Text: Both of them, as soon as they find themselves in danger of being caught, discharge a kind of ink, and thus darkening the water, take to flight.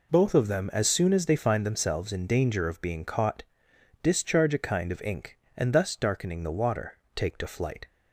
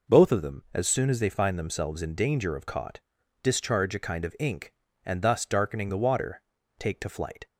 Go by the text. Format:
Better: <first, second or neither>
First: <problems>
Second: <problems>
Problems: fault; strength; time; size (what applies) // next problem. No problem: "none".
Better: first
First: none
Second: skips "being"; at 2.6 s